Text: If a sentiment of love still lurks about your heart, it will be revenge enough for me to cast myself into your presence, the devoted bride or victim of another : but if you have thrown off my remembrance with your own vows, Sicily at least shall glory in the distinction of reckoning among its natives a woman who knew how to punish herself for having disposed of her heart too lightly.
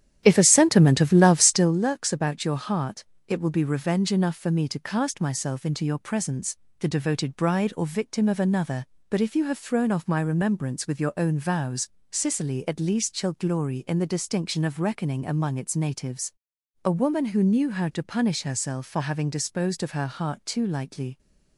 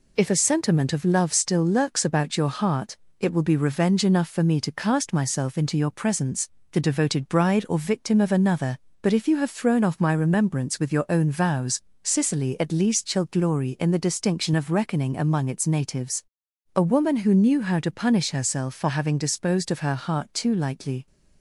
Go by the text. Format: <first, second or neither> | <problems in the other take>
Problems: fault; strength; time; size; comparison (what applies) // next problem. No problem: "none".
second | starts louder than the rest; strong; until 1.8 s; 10.5 dB // pauses between "natives" and "a"; noticeable; at 16.3 s; 0.54 s long; noticeable in the second